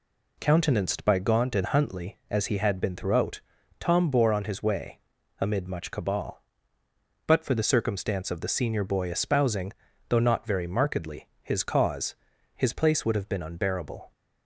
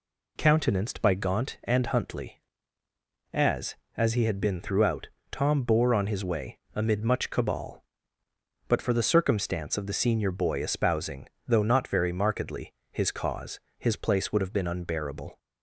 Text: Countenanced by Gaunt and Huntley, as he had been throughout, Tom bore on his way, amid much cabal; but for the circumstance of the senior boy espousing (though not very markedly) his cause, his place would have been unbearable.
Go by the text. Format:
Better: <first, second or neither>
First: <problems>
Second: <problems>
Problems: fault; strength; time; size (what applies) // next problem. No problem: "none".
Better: first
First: none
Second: says "as" twice; at 3.9 s